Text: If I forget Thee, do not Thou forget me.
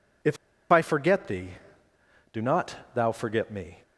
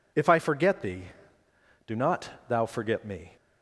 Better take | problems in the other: second | pauses between "If" and "I"; slight; at 0.3 s; 0.35 s long // pauses between "not" and "Thou"; slight; at 2.7 s; 0.18 s long; slight in the second

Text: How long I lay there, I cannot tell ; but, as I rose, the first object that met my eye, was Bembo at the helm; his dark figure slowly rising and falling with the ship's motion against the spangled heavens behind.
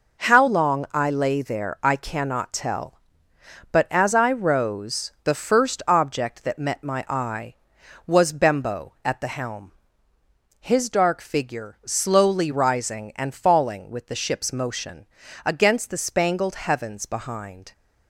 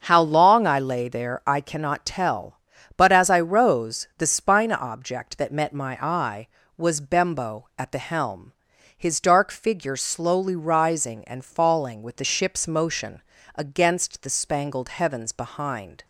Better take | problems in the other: first | starts louder than the rest; until 1.0 s; 6.5 dB // says "spina" for "first"; at 4.2 s // pauses between "motion" and "against"; slight; at 13.2 s; 0.34 s long; also in the first

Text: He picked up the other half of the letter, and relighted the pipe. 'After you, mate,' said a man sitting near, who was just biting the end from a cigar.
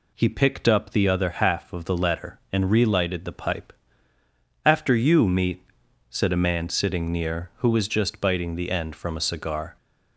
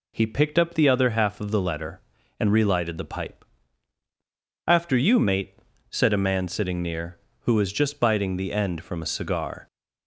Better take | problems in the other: second | says "meat" for "mate"; at 5.2 s

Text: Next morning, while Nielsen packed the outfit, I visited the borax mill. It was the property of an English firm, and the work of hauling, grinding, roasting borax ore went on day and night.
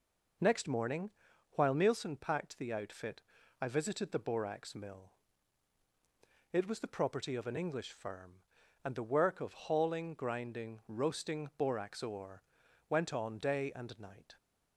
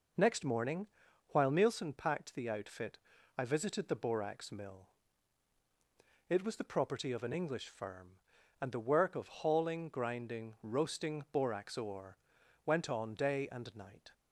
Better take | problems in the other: neither | pauses between "ore" and "went"; noticeable; the same in both

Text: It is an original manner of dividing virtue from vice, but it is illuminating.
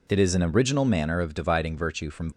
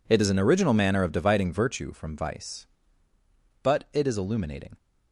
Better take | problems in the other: second | stops before "vice but it is illuminating"; at 2.3 s

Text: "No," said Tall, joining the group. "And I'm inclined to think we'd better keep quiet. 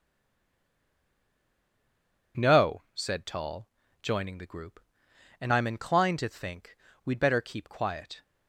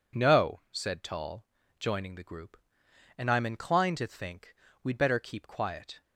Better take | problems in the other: second | stays silent before the first word; until 2.3 s; 2.3 s long // pauses between "think" and "we'd"; slight; at 6.7 s; 0.28 s long; slight in the second

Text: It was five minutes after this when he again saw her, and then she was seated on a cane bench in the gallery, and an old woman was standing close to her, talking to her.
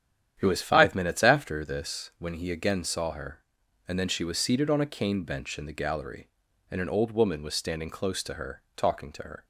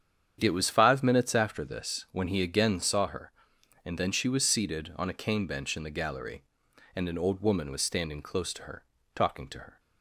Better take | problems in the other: neither | starts louder than the rest; strong; the same in both

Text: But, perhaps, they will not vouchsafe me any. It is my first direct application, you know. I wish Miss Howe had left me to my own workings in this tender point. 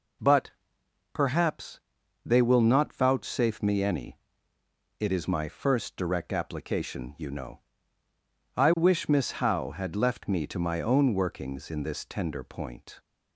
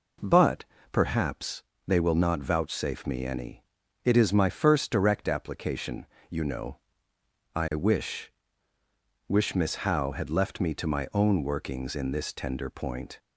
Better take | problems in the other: first | says "wish" twice; at 9.2 s

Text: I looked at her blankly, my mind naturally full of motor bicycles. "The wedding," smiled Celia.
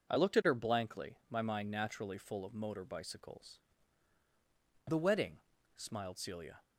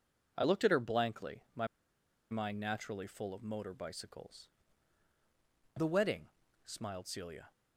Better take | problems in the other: first | pauses between "my" and "mind"; noticeable; at 1.6 s; 0.63 s long

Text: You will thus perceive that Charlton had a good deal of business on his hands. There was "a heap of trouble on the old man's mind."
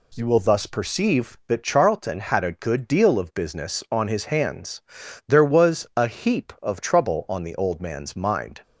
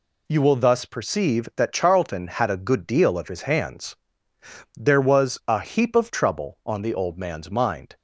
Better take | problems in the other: first | skips "business on"; at 3.2 s

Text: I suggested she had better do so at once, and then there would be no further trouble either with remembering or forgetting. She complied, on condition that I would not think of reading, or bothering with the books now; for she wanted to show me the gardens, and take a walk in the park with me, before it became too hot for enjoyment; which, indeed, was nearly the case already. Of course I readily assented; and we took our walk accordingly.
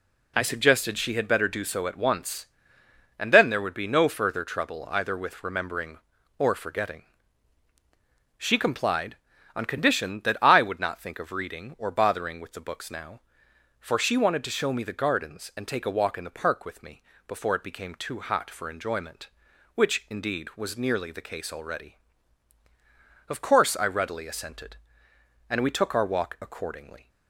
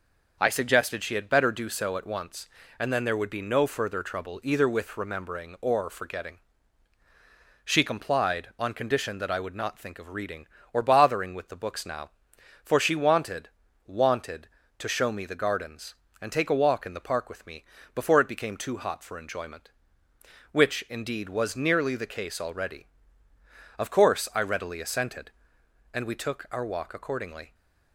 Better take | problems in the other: first | says "wanted" twice; at 13.8 s

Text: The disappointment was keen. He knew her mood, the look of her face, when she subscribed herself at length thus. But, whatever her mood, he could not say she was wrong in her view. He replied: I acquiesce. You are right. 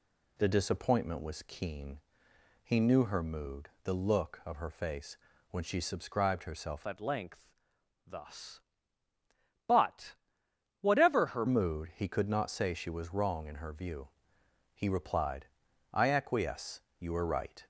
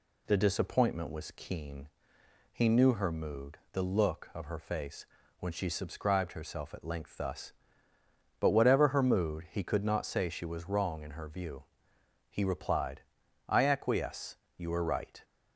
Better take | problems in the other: second | changes voice from "at" to "her"; from 6.8 to 11.4 s; 4.6 s long // pauses between "length" and "thus"; noticeable; at 7.5 s; 0.52 s long

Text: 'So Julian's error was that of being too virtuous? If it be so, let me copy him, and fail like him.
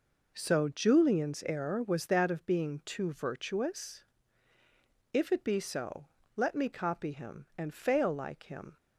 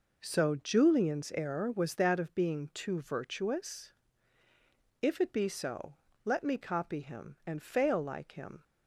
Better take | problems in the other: neither | none

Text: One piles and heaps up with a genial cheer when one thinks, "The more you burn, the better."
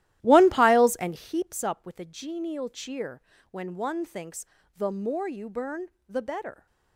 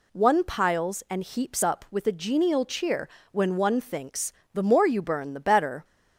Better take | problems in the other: second | starts louder than the rest; strong; until 1.3 s; 14.5 dB // pauses between "cheer" and "when"; slight; at 3.1 s; 0.32 s long; slight in the second

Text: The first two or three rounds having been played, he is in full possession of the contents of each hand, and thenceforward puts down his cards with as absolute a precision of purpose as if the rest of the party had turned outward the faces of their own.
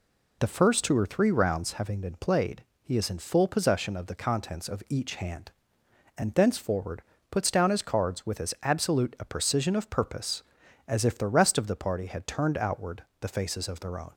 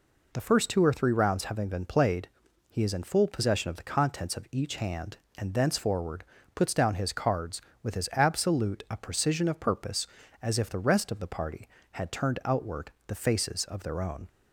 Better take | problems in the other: neither | pauses between "thenceforward" and "puts"; slight; the same in both // pauses between "outward" and "the"; slight; the same in both

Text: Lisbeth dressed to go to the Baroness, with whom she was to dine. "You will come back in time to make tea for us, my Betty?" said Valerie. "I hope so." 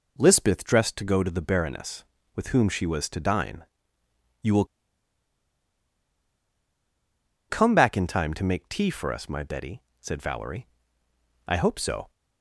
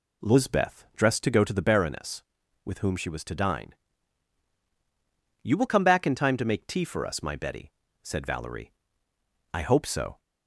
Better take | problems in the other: second | pauses between "will" and "come"; strong; at 4.6 s; 2.8 s long

